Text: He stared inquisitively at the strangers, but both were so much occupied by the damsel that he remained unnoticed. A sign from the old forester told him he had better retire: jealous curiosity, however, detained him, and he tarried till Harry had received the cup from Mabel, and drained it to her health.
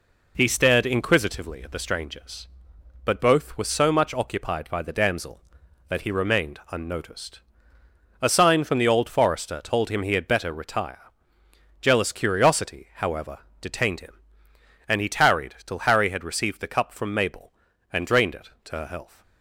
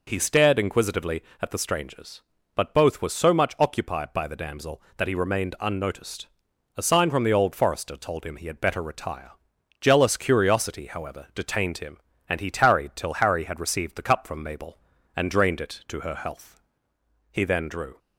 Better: first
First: none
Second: goes on to say "He then drew"; noticeable; from 17.3 s on; 0.68 s long

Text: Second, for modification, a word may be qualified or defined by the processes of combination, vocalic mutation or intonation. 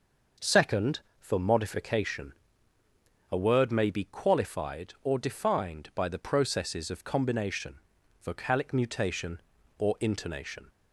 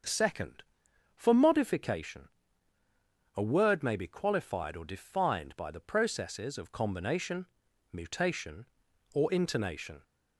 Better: first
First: none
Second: starts louder than the rest; until 1.5 s; 6.5 dB // skips "vocalic"; at 7.6 s

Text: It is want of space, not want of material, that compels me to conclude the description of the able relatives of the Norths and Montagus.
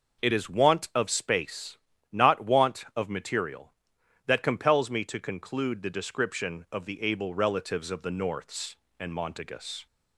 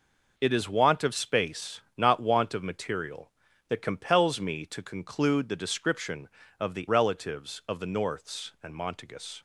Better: first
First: none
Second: skips "able"; at 6.8 s

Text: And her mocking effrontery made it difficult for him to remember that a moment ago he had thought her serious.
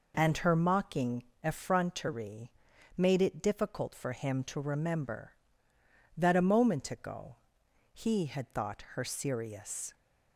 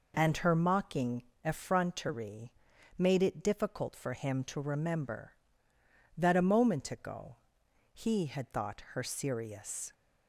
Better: neither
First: pauses between "mocking" and "effrontery"; slight; at 1.2 s; 0.20 s long // pauses between "effrontery" and "made"; at 2.5 s; 0.44 s long // pauses between "ago" and "he"; noticeable; at 7.3 s; 0.56 s long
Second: pauses between "mocking" and "effrontery"; slight; at 1.2 s; 0.22 s long // pauses between "effrontery" and "made"; at 2.5 s; 0.44 s long // pauses between "ago" and "he"; noticeable; at 7.3 s; 0.56 s long

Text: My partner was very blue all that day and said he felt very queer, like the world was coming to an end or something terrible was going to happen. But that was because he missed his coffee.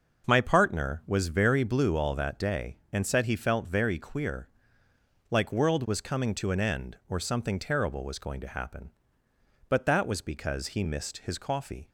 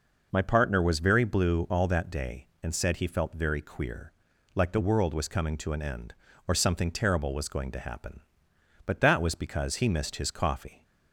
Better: second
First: skips "the"; at 5.5 s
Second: none

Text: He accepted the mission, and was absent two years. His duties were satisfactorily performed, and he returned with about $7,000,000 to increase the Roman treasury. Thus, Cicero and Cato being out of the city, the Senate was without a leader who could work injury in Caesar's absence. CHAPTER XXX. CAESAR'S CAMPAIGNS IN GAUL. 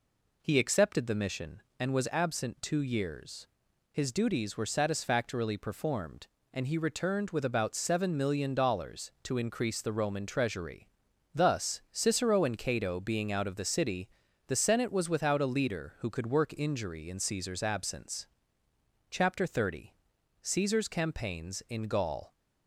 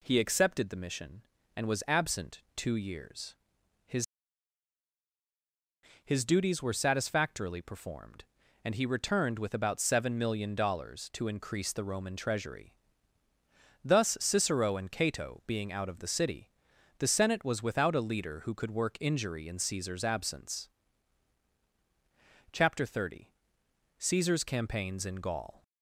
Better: first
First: none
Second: says "His" twice; at 6.0 s

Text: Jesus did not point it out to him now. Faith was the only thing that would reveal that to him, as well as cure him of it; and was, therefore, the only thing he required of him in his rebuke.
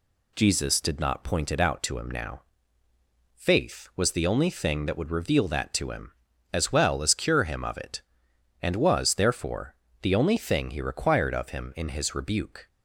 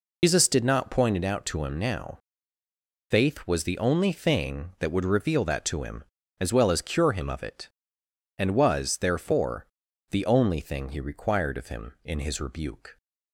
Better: first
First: none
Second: loses the start of "Jesus"; at 0.2 s; 130 ms

